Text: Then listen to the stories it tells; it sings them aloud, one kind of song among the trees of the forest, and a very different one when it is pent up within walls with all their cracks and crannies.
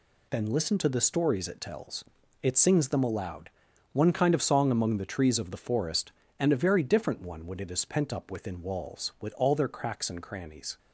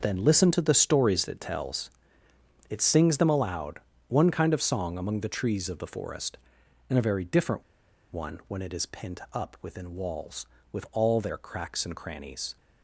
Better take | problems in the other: first | starts louder than the rest; noticeable; until 1.0 s; 6 dB // pauses between "different" and "one"; noticeable; at 7.6 s; 0.49 s long

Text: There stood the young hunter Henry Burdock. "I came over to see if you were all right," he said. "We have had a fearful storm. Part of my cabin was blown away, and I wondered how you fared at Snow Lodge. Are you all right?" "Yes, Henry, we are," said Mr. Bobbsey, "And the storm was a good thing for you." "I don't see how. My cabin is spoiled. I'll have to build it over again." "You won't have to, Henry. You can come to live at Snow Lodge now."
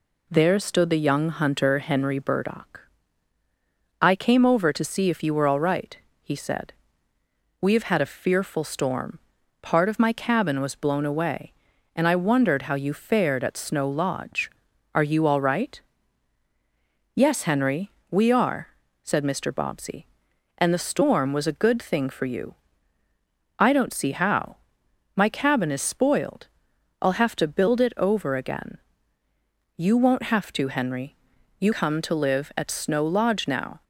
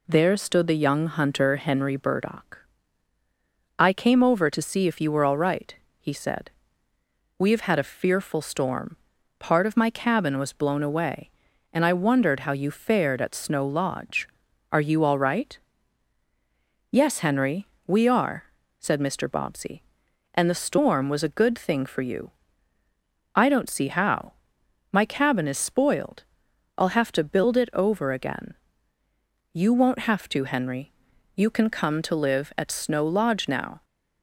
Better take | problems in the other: second | skips "can"; at 31.7 s

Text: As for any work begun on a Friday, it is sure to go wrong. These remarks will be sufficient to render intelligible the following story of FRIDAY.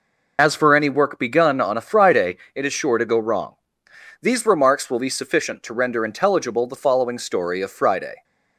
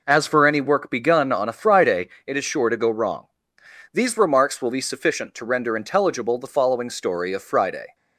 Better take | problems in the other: second | loses the start of "As"; at 0.3 s; 55 ms

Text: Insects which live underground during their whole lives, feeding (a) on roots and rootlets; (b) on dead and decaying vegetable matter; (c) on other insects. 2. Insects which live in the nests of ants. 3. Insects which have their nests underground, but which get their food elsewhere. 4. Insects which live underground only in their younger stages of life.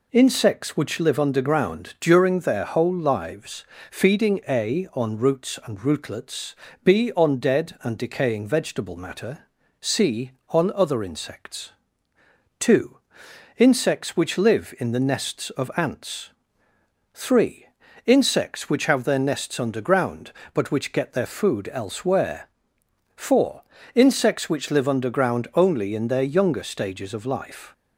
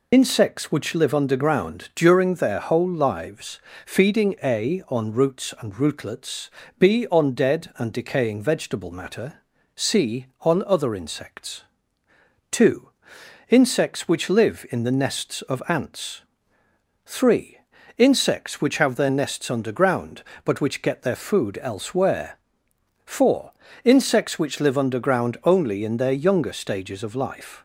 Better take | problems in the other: first | loses the start of "Insects"; at 0.1 s; 65 ms

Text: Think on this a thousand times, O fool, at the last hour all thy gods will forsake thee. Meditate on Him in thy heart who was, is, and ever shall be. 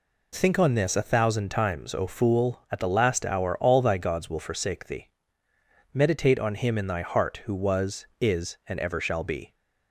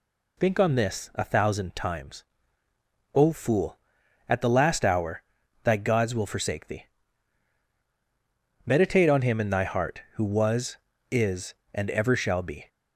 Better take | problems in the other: first | skips "all"; at 5.4 s

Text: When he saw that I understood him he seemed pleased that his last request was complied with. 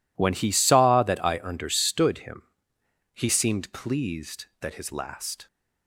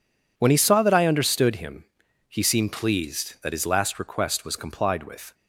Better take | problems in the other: second | pauses between "him" and "he"; noticeable; at 2.4 s; 0.70 s long; also in the second // stops before "request was complied with"; at 5.4 s

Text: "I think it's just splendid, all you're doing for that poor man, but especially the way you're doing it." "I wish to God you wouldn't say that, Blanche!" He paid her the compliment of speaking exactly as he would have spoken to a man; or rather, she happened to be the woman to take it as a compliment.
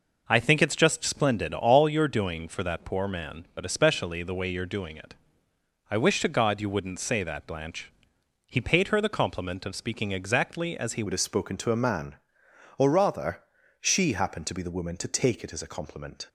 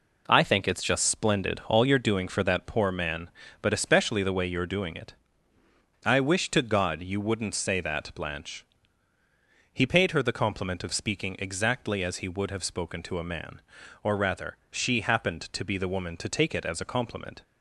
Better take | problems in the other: second | changes voice at "would"; from 11.0 s on; 5.2 s long

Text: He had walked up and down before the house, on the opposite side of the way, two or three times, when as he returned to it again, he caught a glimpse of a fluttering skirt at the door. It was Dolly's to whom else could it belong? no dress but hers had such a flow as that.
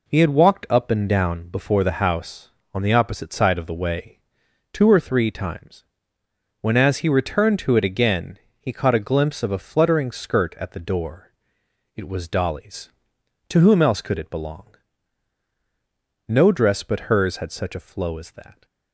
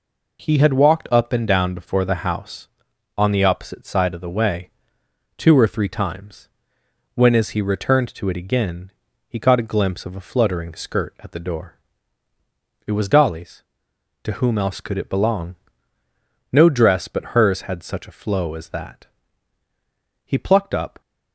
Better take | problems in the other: first | goes on to say "He plucked up"; noticeable; from 20.2 s on; 0.76 s long

